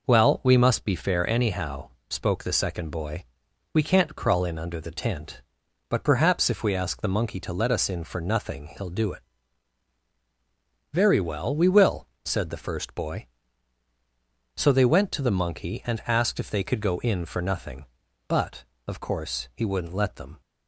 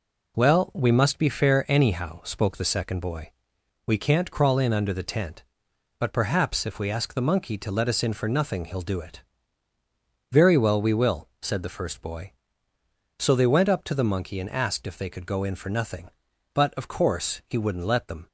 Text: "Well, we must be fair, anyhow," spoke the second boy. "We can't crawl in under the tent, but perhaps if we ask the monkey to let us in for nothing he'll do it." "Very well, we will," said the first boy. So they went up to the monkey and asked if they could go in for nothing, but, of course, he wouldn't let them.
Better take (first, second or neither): second